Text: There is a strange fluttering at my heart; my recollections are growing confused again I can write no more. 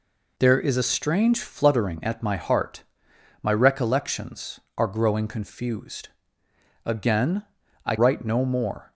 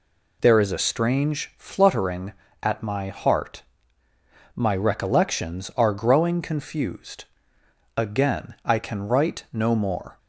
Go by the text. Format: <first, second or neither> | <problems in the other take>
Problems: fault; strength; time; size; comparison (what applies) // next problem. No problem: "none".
second | pauses between "confused" and "again"; noticeable; at 6.1 s; 0.74 s long; noticeable in the second // pauses between "again" and "I"; at 7.4 s; 0.42 s long // skips "can"; at 7.9 s